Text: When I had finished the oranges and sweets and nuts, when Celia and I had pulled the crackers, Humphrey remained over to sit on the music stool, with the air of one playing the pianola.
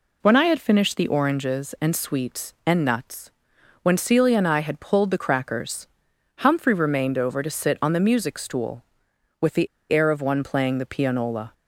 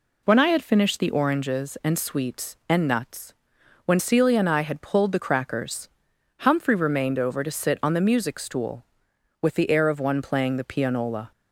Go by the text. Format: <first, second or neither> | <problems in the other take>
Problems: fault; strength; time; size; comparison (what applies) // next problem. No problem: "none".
second | pauses between "the" and "air"; slight; at 9.6 s; 0.25 s long